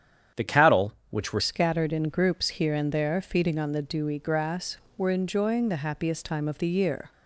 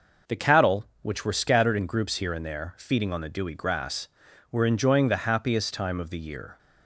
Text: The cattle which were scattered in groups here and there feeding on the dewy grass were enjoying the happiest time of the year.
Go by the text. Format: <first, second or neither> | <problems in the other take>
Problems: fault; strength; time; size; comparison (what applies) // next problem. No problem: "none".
second | starts louder than the rest; strong; until 1.5 s; 9 dB // changes voice at "scattered"; from 1.3 s on; 5.8 s long